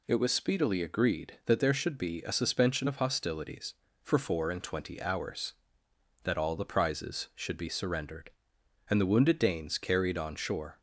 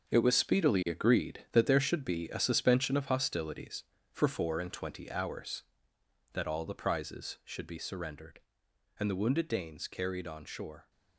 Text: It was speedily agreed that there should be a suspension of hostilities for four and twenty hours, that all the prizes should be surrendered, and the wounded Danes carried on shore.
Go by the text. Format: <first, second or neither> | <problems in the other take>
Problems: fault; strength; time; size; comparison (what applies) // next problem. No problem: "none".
first | gets quieter; strong; throughout; 10 dB